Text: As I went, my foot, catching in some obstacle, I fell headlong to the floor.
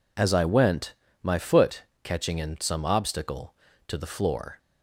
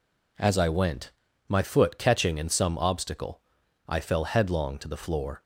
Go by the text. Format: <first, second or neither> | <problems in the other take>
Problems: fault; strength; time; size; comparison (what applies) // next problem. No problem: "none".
second | skips "I fell headlong"; at 3.7 s